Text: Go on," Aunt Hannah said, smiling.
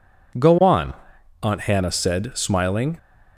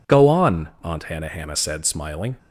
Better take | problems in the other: first | says "Hannah" twice; at 1.2 s

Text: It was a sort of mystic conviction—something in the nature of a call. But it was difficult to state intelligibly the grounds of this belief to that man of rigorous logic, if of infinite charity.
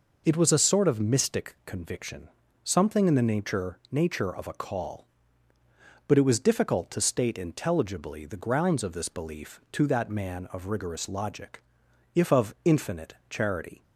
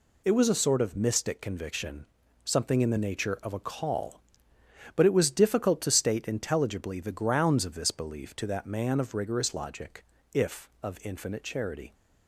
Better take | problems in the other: second | says "nature" twice; at 3.8 s // pauses between "infinite" and "charity"; slight; at 13.1 s; 0.16 s long

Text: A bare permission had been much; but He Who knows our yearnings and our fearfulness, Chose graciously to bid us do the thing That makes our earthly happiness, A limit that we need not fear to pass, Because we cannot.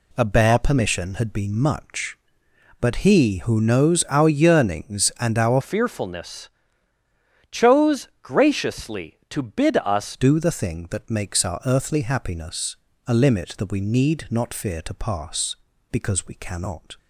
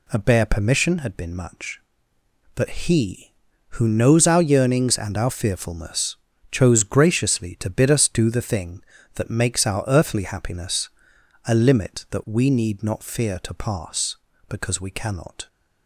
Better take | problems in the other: second | changes voice from "fearfulness" to "us"; from 5.6 to 10.1 s; 4.5 s long

